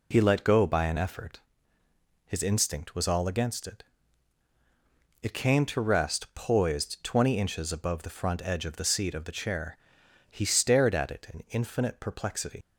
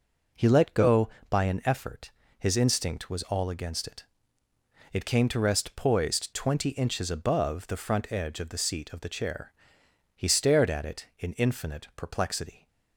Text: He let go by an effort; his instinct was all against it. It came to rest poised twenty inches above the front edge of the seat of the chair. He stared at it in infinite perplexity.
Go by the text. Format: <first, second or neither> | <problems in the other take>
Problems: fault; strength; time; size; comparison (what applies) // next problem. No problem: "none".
second | leaves "perplexity" unfinished; at 12.6 s; 95 ms